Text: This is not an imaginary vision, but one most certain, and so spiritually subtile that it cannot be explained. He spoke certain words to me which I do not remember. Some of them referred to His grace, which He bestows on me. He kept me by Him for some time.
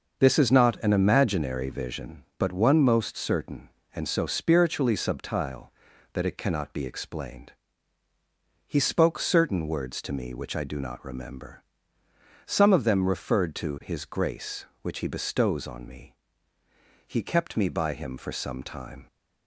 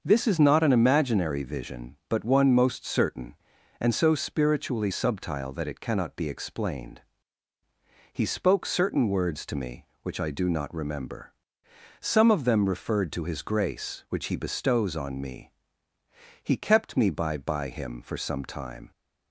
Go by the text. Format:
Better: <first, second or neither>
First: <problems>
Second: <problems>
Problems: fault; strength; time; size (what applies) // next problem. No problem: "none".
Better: first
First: starts louder than the rest; noticeable; until 1.2 s; 6 dB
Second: starts louder than the rest; until 1.0 s; 6.5 dB // says "by" twice; at 17.3 s